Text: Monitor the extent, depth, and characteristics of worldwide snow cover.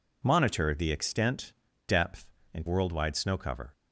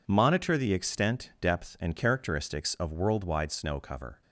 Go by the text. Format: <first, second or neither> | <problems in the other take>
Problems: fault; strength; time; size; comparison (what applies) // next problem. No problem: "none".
second | skips "characteristics of"; at 2.6 s